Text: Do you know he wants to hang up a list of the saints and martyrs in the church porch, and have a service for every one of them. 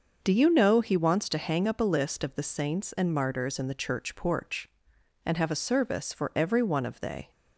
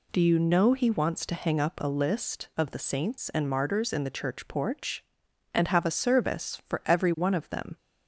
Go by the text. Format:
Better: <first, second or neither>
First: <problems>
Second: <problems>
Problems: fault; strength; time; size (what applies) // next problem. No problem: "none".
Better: second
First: starts louder than the rest; noticeable; until 1.2 s; 6 dB // says "they" for "them"; at 7.0 s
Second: none